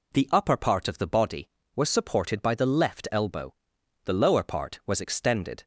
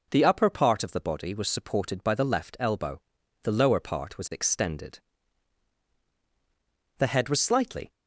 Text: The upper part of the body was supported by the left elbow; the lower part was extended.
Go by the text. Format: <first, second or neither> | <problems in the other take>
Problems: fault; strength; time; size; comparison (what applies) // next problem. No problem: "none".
first | goes on to say "The head was slightly"; noticeable; from 6.9 s on; 0.94 s long